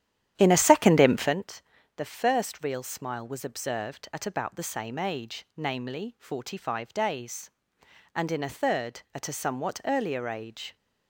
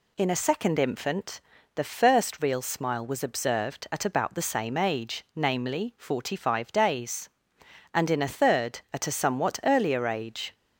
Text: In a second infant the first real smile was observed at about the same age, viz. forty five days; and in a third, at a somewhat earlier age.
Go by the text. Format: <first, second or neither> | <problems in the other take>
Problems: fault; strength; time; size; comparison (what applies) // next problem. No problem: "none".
second | starts louder than the rest; strong; until 1.4 s; 11 dB // pauses between "infant" and "the"; slight; at 1.6 s; 0.34 s long; slight in the second